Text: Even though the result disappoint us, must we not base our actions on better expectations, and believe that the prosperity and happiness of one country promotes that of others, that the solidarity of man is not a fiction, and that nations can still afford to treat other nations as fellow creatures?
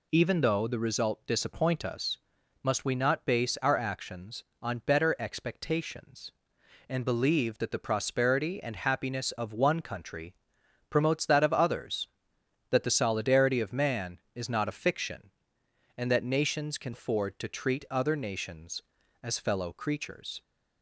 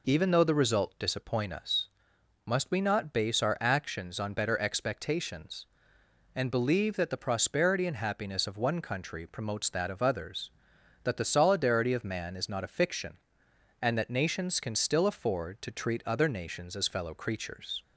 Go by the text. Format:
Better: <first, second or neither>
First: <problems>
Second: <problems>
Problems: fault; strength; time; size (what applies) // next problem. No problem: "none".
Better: second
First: pauses between "country" and "promotes"; noticeable; at 10.3 s; 0.56 s long // skips "still"; at 16.9 s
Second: none